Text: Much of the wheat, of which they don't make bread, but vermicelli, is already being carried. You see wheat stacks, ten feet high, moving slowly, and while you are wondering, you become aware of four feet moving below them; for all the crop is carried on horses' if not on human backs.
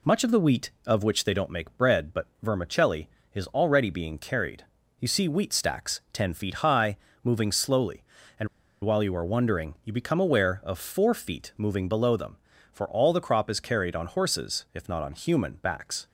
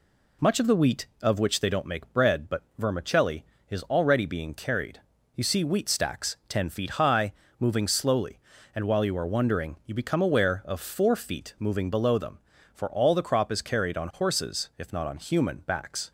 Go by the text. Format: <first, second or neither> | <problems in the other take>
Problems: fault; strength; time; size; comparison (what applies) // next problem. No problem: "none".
second | pauses between "but" and "vermicelli"; slight; at 2.2 s; 0.16 s long; slight in the second // pauses between "and" and "while"; at 8.4 s; 0.36 s long